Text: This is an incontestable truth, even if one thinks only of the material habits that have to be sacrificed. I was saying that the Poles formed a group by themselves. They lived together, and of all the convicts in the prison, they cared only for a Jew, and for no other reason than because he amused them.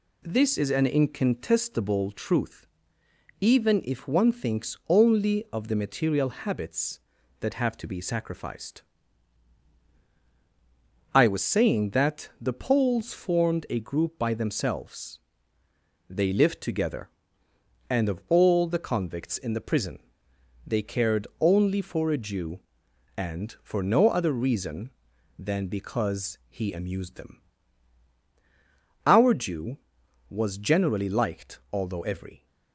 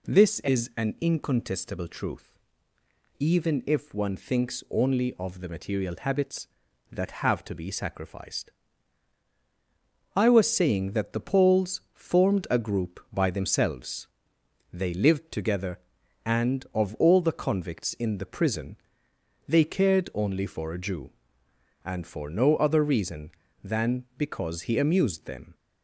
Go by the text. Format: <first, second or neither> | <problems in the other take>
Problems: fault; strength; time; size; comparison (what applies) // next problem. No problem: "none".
second | goes on to say "Our Jew was generally liked although every"; strong; from 29.0 s on; 3.4 s long